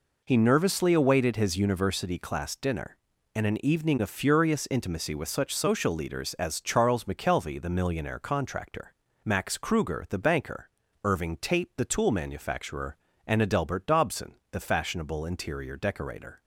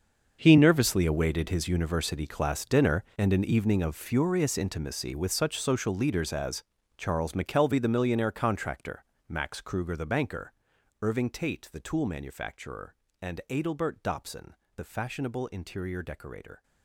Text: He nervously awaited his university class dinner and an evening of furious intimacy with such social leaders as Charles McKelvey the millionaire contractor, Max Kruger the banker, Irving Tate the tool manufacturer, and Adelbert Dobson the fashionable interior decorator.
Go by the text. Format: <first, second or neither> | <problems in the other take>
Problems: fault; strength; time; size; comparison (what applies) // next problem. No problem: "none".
first | gets quieter; strong; throughout; 15 dB // pauses between "as" and "Charles"; slight; at 6.6 s; 0.34 s long // pauses between "Dobson" and "the"; slight; at 14.5 s; 0.22 s long; slight in the first